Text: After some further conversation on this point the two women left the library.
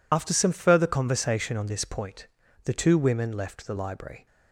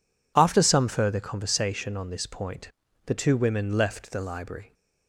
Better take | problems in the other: second | loses the start of "After"; at 0.1 s; 55 ms // pauses between "point" and "the"; at 2.2 s; 0.38 s long; slight in the second

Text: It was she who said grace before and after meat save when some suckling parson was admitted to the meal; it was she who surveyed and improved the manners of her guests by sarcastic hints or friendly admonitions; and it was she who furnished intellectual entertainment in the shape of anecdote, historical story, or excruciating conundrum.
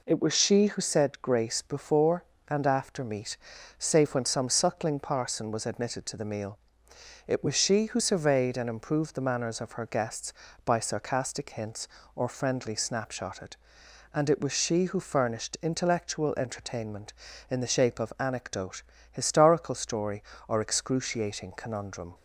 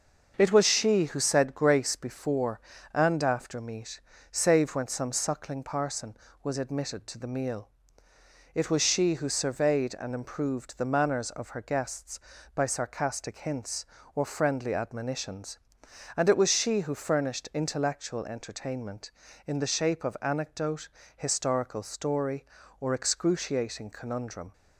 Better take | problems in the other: second | pauses between "meat" and "save"; at 3.3 s; 0.40 s long; slight in the second // says "snapshotted" for "admonitions"; at 12.7 s

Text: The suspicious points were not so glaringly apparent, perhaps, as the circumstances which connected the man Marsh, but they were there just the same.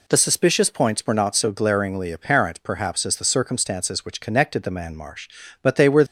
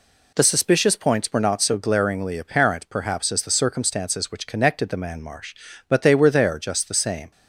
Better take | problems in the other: second | stops before "there just the same"; at 6.0 s

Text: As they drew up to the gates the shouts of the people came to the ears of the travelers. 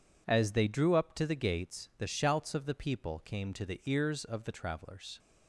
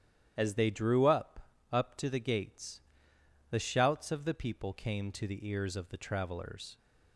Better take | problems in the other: first | starts louder than the rest; strong; until 1.4 s; 10.5 dB // says "up" twice; at 1.7 s // pauses between "gates" and "the"; noticeable; at 2.7 s; 0.70 s long

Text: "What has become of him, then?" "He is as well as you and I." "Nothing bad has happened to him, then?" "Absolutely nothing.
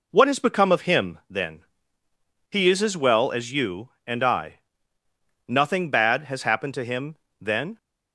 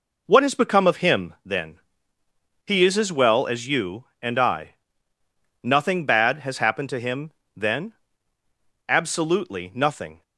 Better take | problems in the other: second | stops before "Absolutely nothing"; at 7.7 s

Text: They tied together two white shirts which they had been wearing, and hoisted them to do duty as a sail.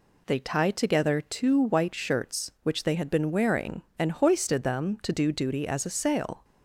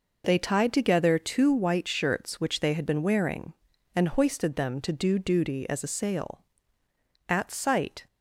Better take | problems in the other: first | goes on to say "At sight"; noticeable; from 7.2 s on; 0.78 s long

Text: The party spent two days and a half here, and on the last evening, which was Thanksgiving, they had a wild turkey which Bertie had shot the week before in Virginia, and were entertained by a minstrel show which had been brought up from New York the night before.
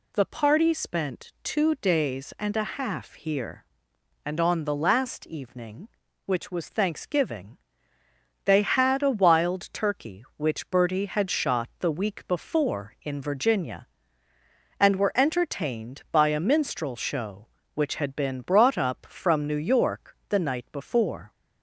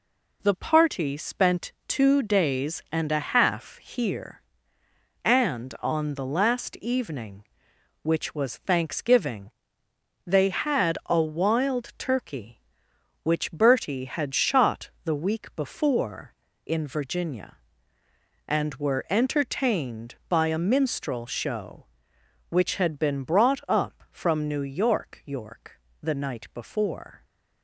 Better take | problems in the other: first | pauses between "shot" and "the"; slight; at 14.8 s; 0.16 s long // says "York" twice; at 25.2 s

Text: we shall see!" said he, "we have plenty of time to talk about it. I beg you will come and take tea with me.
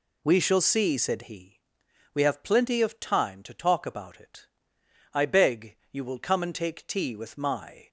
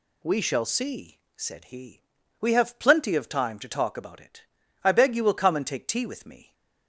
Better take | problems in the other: second | says "my" for "me"; at 7.3 s

